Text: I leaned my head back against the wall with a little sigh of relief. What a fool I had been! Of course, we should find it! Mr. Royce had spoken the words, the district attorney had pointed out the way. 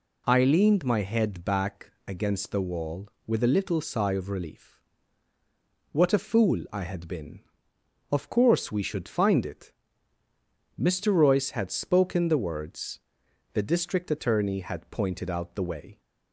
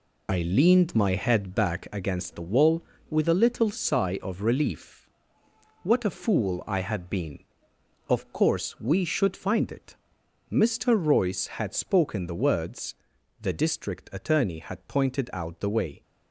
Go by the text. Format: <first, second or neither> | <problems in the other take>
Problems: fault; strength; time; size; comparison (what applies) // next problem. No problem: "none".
first | loses the start of "I"; at 0.2 s; 25 ms